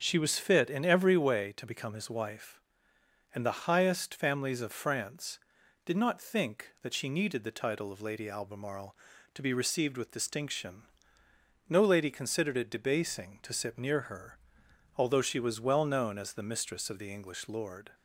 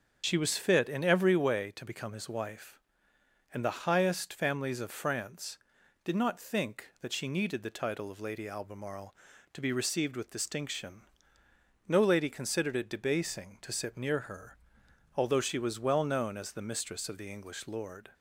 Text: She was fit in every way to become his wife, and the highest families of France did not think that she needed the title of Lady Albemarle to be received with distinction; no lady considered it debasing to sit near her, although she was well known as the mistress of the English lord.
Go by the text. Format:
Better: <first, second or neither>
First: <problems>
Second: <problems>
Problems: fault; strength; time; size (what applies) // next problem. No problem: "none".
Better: first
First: starts louder than the rest; until 1.0 s; 7 dB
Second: loses the start of "She"; at 0.2 s; 45 ms // starts louder than the rest; until 1.2 s; 7 dB